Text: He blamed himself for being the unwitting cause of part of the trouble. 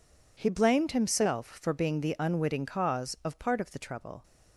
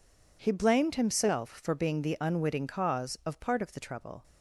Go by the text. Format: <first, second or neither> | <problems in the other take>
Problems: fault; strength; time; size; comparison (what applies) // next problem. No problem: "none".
neither | none